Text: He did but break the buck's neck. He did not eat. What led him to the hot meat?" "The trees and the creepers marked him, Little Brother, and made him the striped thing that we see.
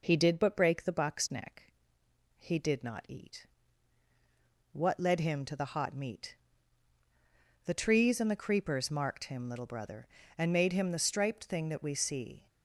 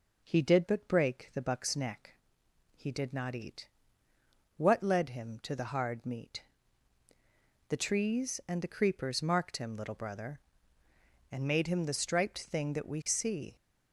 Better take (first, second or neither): first